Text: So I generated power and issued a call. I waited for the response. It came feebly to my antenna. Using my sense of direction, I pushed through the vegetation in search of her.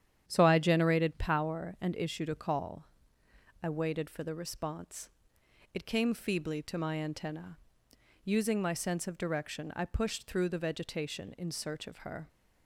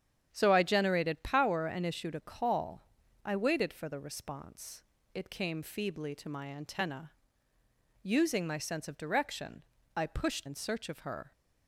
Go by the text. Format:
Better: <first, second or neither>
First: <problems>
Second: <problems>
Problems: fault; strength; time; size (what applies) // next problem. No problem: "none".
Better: first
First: starts louder than the rest; strong; until 1.2 s; 9.5 dB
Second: starts louder than the rest; strong; until 1.3 s; 9 dB // skips "through the vegetation"; at 10.4 s